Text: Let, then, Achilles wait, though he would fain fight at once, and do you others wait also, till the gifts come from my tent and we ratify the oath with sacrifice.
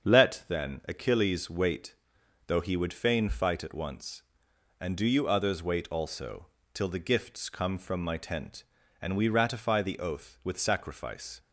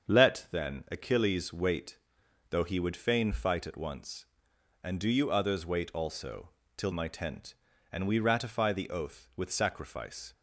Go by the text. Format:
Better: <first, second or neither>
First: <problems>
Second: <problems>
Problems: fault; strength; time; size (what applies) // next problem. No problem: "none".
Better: first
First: starts louder than the rest; until 1.1 s; 7 dB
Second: starts louder than the rest; until 1.2 s; 7 dB // skips "the gifts come from"; at 6.9 s